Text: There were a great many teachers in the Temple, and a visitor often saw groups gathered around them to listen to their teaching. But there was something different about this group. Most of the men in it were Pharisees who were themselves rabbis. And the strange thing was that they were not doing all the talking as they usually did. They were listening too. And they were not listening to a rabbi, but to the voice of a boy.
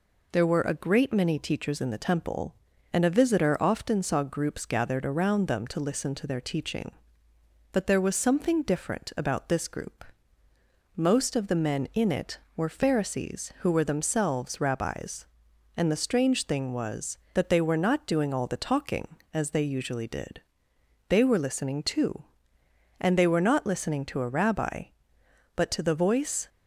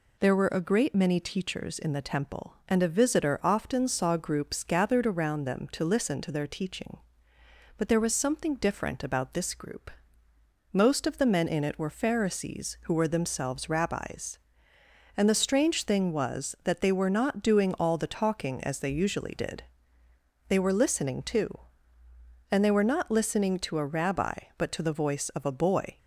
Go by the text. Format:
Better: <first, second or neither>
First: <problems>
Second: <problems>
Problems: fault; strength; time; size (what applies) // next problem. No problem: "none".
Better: second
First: stops before "of a boy"; at 26.4 s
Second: none